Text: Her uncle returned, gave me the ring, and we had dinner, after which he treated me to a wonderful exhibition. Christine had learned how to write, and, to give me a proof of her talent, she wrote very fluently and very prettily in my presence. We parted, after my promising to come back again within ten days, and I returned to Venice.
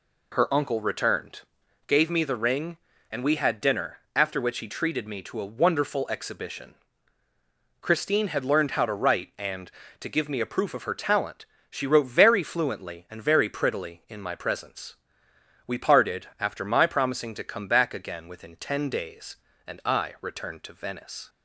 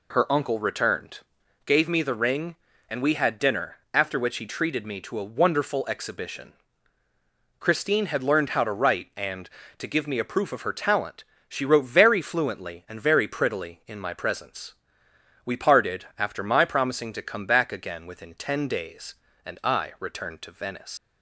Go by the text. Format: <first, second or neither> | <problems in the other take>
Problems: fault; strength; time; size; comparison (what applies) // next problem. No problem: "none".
first | leaves "Venice" unfinished; at 20.9 s; 100 ms